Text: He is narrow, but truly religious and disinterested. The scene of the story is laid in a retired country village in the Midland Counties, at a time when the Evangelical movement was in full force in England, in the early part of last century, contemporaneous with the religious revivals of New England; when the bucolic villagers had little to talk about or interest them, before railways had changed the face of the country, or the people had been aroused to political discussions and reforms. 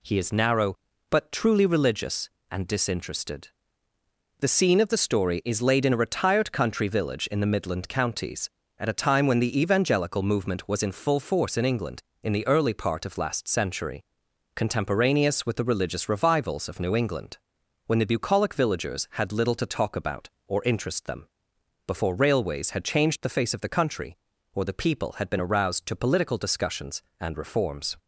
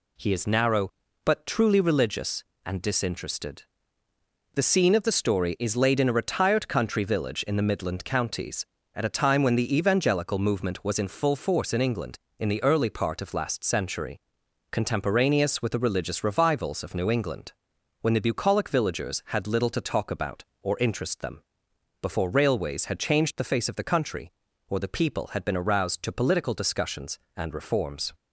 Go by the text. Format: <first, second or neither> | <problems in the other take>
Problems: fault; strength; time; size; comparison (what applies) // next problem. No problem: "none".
neither | none